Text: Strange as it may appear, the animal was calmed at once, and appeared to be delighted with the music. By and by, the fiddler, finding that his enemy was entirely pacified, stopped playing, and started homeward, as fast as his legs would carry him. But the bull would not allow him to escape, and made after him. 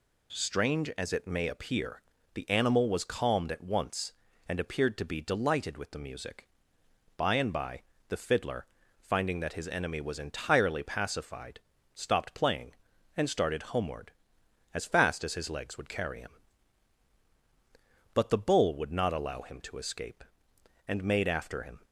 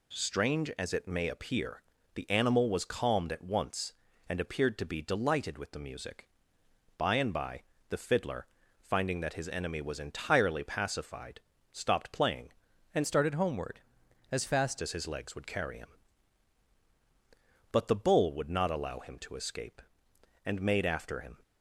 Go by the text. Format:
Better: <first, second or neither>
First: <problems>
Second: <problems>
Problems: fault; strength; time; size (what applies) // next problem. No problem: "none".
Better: first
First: none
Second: changes voice from "started" to "fast"; from 13.0 to 14.8 s; 1.8 s long